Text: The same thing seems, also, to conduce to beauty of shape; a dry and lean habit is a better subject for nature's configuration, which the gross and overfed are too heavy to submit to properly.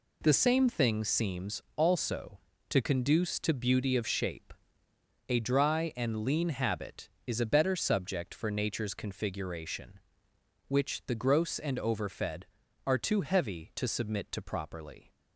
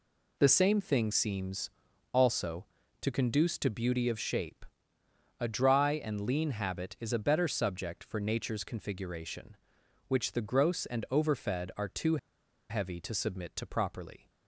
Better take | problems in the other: first | pauses between "too" and "heavy"; noticeable; at 12.1 s; 0.52 s long

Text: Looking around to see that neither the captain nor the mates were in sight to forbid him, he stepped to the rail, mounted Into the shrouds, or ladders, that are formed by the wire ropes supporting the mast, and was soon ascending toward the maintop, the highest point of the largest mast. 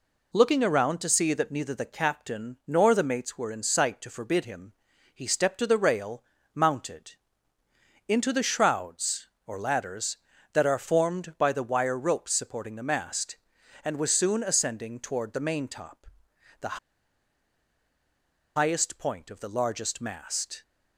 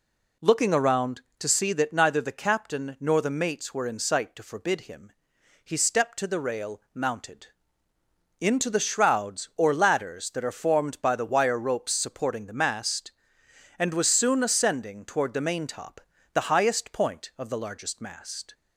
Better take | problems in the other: second | pauses between "mounted" and "Into"; noticeable; at 7.1 s; 0.96 s long; noticeable in the second // pauses between "the" and "highest"; strong; at 16.7 s; 1.7 s long

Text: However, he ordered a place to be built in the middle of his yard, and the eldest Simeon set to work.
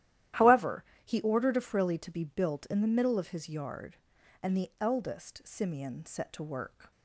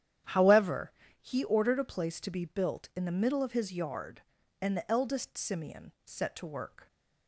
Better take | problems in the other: second | starts louder than the rest; strong; until 1.5 s; 13 dB; strong in the second // says "frilly" for "place"; at 1.6 s

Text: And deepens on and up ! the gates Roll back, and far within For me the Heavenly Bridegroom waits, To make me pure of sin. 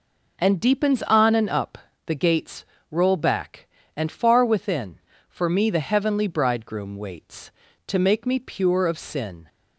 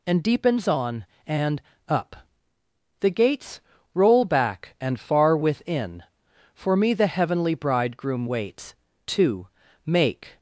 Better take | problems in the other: first | pauses between "and" and "up"; slight; at 1.6 s; 0.26 s long // pauses between "gates" and "Roll"; slight; at 3.5 s; 0.34 s long; slight in the first // pauses between "To" and "make"; slight; at 9.4 s; 0.36 s long // stops before "me pure of sin"; at 10.3 s

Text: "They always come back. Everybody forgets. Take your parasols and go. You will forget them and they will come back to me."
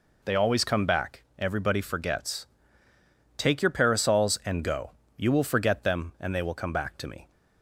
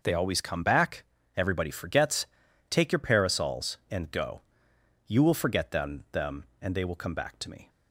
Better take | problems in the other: first | says "them" twice; at 6.1 s

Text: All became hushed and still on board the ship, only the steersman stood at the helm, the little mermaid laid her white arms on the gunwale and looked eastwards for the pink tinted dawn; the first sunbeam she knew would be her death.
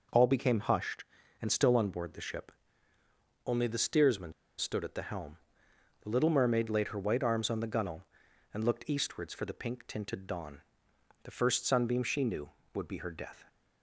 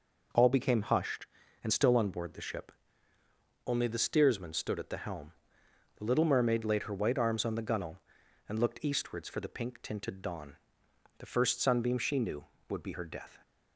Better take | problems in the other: second | pauses between "steersman" and "stood"; slight; at 4.3 s; 0.25 s long

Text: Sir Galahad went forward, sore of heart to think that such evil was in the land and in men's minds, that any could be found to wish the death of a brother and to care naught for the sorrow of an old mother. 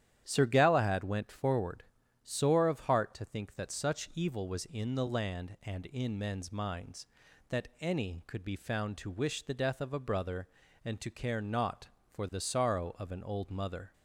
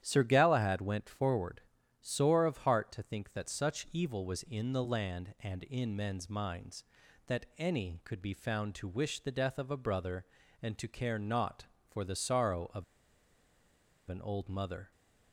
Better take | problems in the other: first | starts louder than the rest; strong; until 1.0 s; 10.5 dB; strong in the first // pauses between "of" and "an"; strong; at 12.8 s; 1.2 s long

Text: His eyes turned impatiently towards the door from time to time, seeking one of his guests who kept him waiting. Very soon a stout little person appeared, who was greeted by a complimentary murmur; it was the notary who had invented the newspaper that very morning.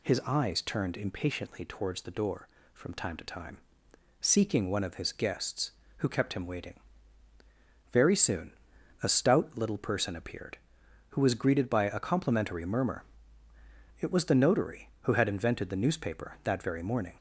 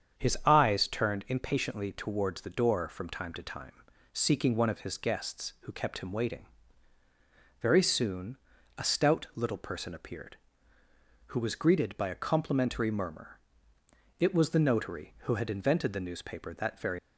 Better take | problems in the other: first | starts louder than the rest; strong; until 1.2 s; 7.5 dB // pauses between "soon" and "a"; at 8.3 s; 0.40 s long; noticeable in the first // stops before "morning"; at 16.9 s

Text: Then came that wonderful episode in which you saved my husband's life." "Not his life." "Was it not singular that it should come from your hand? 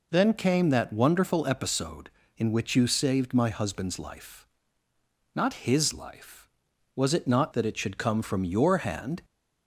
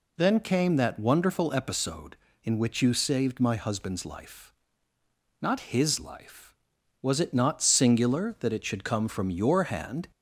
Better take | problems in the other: second | skips "singular"; at 7.5 s

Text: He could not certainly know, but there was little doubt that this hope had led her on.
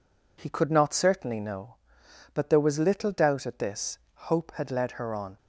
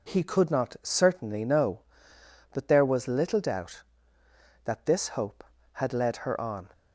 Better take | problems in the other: second | says "at" for "that"; at 3.4 s // pauses between "this" and "hope"; slight; at 3.9 s; 0.18 s long

